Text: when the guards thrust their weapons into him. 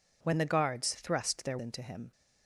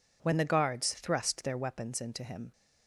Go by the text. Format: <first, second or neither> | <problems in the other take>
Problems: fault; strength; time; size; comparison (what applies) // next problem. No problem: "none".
second | skips "weapons"; at 1.5 s